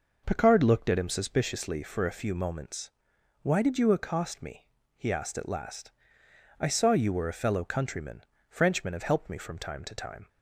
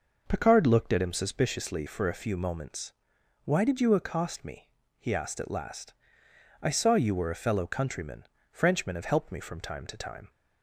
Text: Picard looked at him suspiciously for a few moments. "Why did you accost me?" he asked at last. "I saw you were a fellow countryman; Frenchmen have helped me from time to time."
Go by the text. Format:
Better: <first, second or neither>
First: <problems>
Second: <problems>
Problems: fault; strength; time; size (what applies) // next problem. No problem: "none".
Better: neither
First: none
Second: none